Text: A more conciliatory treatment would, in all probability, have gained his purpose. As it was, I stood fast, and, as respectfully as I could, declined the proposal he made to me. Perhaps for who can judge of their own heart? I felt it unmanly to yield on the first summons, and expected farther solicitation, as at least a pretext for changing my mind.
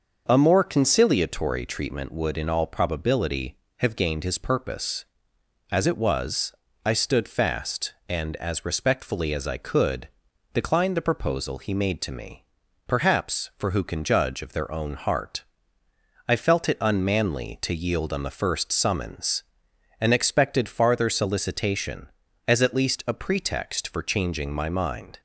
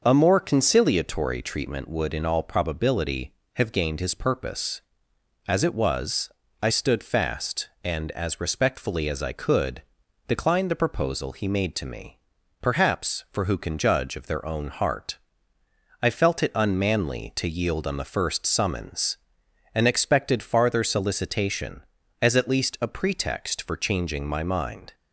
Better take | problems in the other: neither | starts louder than the rest; the same in both

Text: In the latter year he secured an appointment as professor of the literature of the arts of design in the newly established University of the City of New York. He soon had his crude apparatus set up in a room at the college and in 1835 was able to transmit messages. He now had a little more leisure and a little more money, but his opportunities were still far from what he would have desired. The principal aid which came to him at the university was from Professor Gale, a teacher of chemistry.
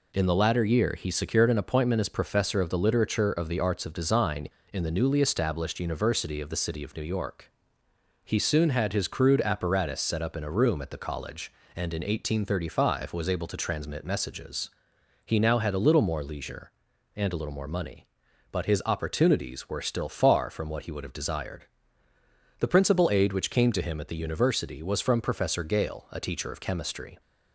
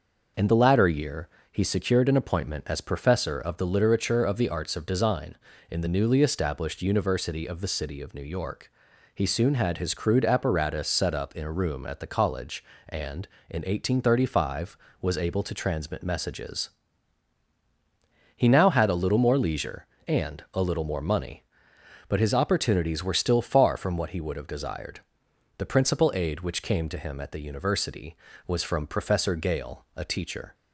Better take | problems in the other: first | pauses between "year" and "he"; slight; at 1.2 s; 0.24 s long // stops before "of chemistry"; at 30.5 s

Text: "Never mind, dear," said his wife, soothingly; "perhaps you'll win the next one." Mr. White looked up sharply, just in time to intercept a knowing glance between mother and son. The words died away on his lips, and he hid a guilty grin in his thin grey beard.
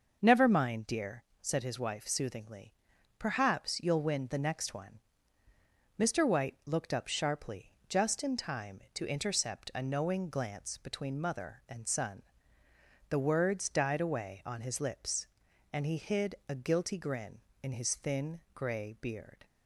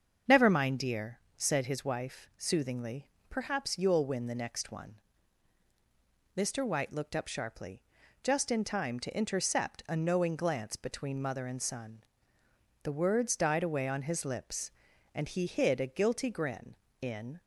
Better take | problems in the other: first | starts louder than the rest; until 1.4 s; 7 dB // stops before "his thin grey beard"; at 17.3 s

